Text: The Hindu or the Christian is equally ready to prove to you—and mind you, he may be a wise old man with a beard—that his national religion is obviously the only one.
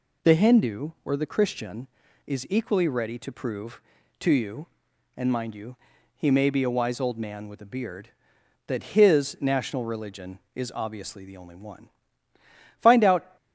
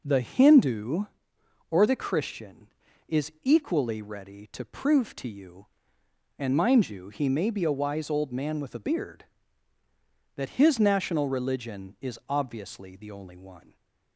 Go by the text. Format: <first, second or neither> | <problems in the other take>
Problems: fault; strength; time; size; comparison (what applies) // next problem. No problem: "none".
second | goes on to say "Find out"; from 12.8 s on; 0.56 s long